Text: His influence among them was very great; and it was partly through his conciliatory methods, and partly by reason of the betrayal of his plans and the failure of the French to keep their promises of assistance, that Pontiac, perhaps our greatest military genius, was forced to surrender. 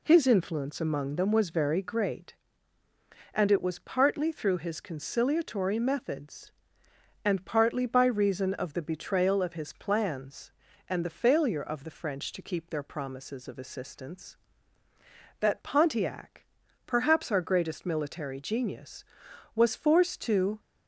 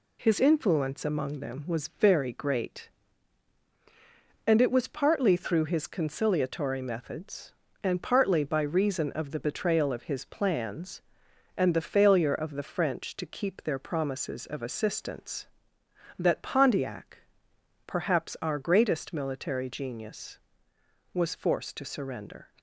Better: second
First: stops before "surrender"; at 20.5 s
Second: none

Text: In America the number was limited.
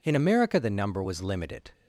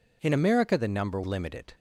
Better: first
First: none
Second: skips "was"; at 1.2 s

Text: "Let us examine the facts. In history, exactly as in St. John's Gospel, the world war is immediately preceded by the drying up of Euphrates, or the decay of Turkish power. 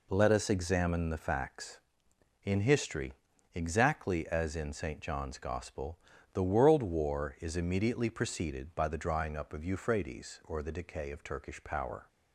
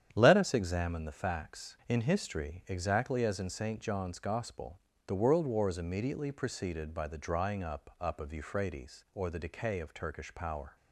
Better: first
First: none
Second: starts louder than the rest; strong; until 1.1 s; 9 dB // says "up" twice; at 8.0 s

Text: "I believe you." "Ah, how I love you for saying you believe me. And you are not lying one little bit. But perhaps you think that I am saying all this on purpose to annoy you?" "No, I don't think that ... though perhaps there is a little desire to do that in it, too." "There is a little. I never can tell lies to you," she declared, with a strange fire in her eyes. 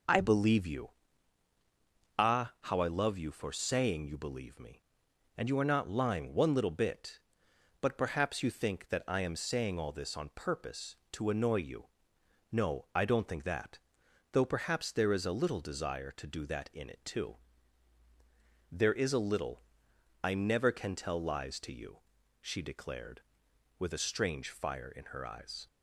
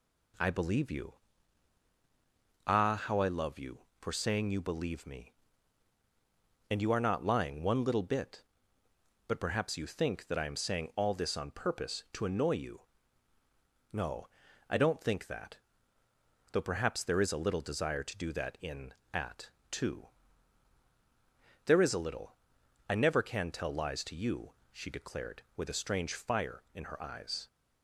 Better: first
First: none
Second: says "at" for "it"; at 19.1 s

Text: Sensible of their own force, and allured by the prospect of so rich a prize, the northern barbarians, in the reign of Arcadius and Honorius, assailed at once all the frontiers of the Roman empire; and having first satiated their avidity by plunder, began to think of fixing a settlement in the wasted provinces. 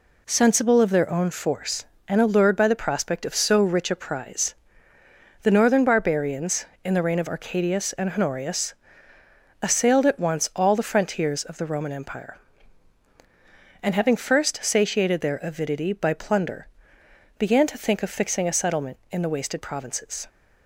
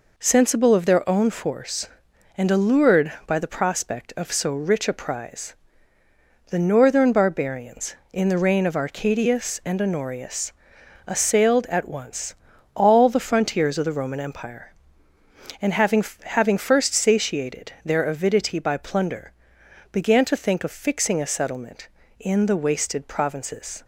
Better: first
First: none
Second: pauses between "once" and "all"; at 12.3 s; 0.40 s long // says "having" twice; at 16.2 s

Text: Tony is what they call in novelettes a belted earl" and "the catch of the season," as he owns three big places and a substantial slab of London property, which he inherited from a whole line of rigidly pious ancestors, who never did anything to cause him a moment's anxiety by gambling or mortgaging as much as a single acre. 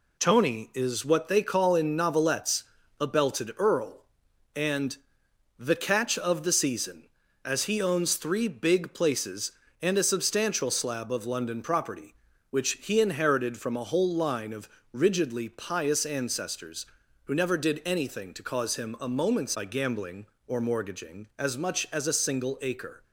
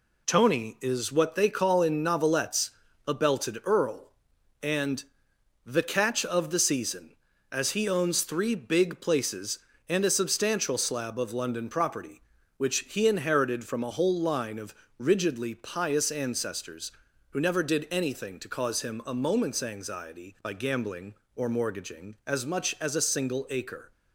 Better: second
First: pauses between "novelettes" and "a"; slight; at 2.6 s; 0.36 s long // pauses between "and" and "the"; noticeable; at 4.9 s; 0.62 s long // pauses between "of" and "rigidly"; slight; at 14.6 s; 0.24 s long // skips "anxiety"; at 19.5 s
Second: pauses between "novelettes" and "a"; slight; at 2.7 s; 0.36 s long // pauses between "and" and "the"; noticeable; at 5.0 s; 0.62 s long // pauses between "of" and "rigidly"; slight; at 14.7 s; 0.24 s long

